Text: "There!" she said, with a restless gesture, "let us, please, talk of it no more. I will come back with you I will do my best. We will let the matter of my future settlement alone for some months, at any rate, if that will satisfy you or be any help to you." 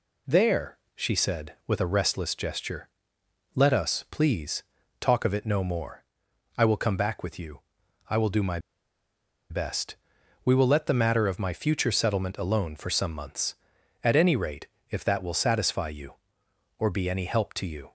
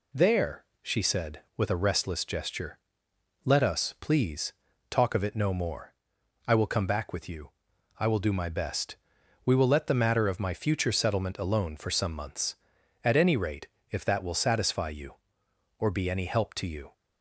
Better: second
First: pauses between "you" and "I"; noticeable; at 7.6 s; 0.48 s long // pauses between "my" and "best"; noticeable; at 8.5 s; 0.91 s long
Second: pauses between "you" and "I"; noticeable; at 7.5 s; 0.48 s long

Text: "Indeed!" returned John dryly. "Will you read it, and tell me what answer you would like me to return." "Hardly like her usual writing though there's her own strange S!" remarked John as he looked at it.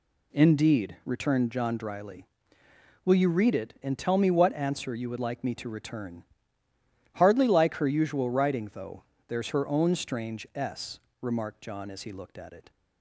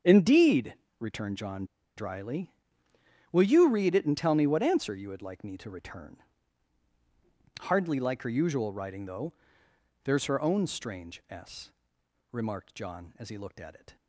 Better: first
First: pauses between "though" and "there's"; slight; at 9.0 s; 0.24 s long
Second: starts louder than the rest; until 1.2 s; 7 dB // pauses between "John" and "dryly"; slight; at 1.6 s; 0.30 s long // pauses between "though" and "there's"; noticeable; at 9.3 s; 0.70 s long

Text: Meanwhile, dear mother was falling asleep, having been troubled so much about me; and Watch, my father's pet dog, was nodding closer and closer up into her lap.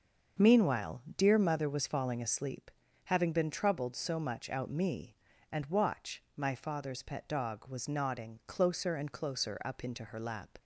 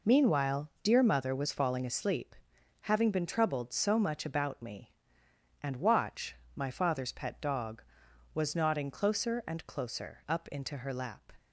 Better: second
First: starts louder than the rest; until 1.5 s; 6.5 dB // says "out" for "about"; at 4.4 s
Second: none

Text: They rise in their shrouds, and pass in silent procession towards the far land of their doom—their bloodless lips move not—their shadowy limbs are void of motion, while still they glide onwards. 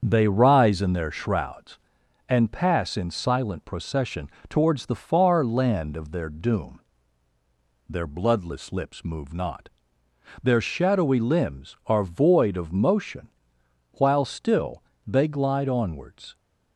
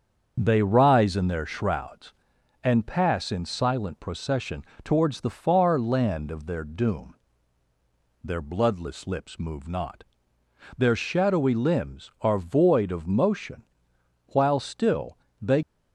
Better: first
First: starts louder than the rest; until 1.0 s; 7 dB // pauses between "procession" and "towards"; slight; at 4.2 s; 0.22 s long // pauses between "still" and "they"; slight; at 14.8 s; 0.24 s long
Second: starts louder than the rest; until 1.4 s; 7 dB // pauses between "procession" and "towards"; slight; at 4.6 s; 0.22 s long // pauses between "still" and "they"; slight; at 15.1 s; 0.24 s long // stops before "glide onwards"; at 15.6 s

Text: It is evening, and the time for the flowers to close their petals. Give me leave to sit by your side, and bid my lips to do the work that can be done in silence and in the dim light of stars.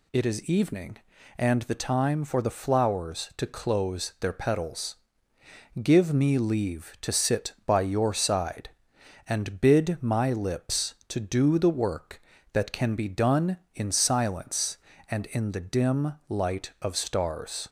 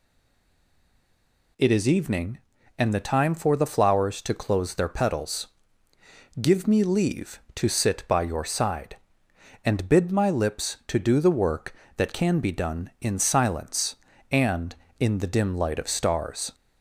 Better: first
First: none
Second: stays silent before the first word; noticeable; until 1.5 s; 1.5 s long

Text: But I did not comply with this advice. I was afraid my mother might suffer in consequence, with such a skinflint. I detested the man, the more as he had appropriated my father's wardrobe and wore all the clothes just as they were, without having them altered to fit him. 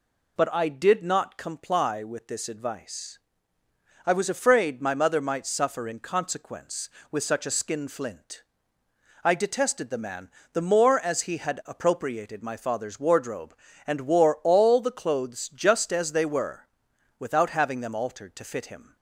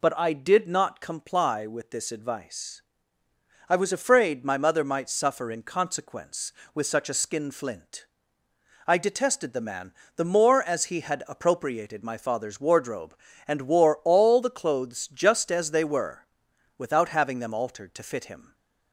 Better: neither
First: none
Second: none

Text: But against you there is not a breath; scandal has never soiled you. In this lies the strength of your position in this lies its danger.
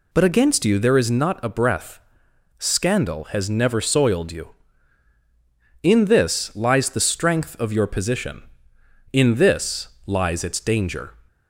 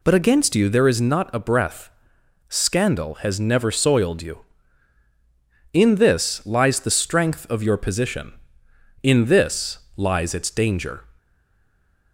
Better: first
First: pauses between "this" and "lies"; slight; at 9.8 s; 0.18 s long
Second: pauses between "this" and "lies"; slight; at 9.7 s; 0.18 s long // stays silent after the last word; slight; from 11.1 s on; 1.0 s long

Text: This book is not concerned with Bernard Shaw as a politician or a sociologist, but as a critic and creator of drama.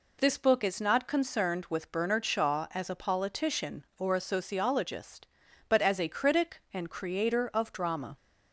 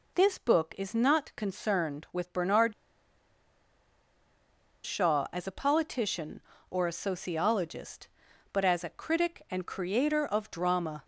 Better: first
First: none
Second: pauses between "Bernard" and "Shaw"; strong; at 2.7 s; 2.1 s long

